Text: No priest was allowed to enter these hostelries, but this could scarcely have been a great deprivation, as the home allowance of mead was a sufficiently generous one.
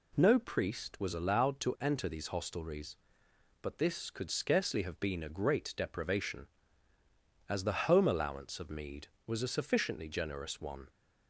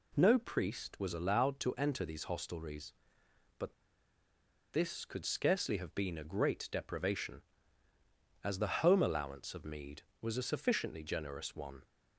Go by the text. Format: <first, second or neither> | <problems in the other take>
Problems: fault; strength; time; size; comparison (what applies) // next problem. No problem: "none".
first | pauses between "but" and "this"; at 3.7 s; 0.99 s long